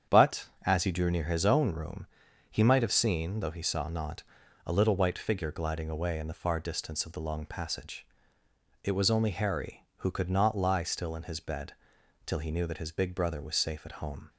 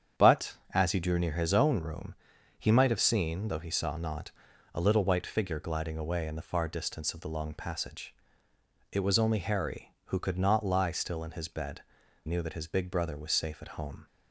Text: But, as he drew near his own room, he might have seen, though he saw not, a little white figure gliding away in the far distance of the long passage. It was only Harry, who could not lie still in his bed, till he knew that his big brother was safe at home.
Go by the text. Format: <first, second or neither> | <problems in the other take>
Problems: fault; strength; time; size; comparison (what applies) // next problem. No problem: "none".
first | starts louder than the rest; strong; until 1.3 s; 8 dB; strong in the first // skips "till he"; at 12.0 s